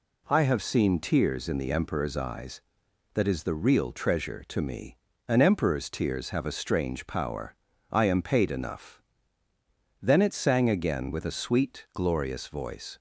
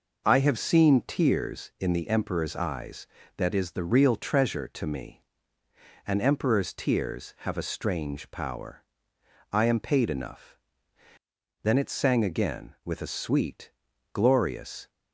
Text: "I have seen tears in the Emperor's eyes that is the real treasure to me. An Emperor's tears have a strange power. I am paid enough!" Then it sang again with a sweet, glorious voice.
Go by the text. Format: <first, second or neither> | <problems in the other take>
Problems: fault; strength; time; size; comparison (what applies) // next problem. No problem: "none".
first | stops before "voice"; at 14.8 s